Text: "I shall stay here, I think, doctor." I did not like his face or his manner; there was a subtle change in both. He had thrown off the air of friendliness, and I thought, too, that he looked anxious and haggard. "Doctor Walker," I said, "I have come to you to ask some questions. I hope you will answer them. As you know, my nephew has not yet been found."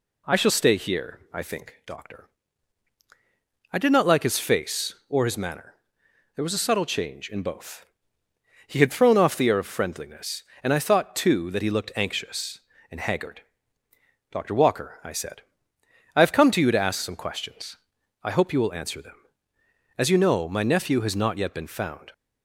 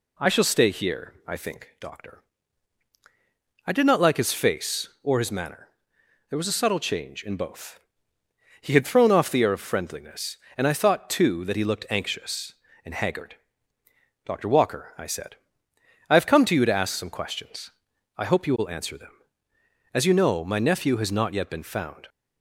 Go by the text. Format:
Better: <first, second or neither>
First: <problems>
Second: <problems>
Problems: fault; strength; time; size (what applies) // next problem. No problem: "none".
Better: neither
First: none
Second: none